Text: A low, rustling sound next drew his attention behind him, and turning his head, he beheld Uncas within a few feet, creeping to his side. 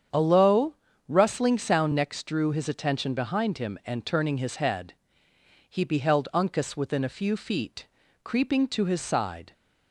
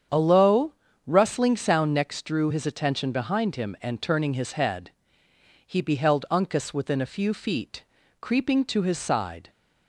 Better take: neither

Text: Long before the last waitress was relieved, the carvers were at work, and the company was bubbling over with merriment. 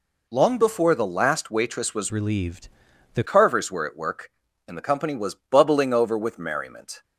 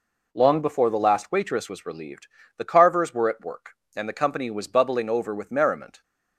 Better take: second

